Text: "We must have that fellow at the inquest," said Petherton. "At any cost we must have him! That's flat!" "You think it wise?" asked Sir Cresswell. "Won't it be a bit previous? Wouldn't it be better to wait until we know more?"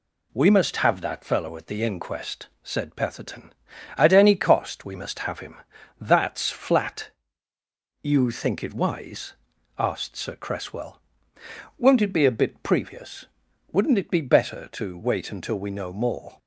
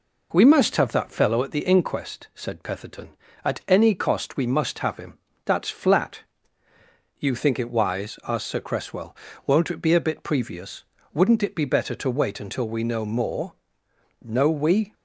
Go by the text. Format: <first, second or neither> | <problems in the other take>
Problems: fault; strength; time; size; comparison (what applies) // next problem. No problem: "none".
first | goes on to say "No we"; noticeable; from 14.2 s on; 0.72 s long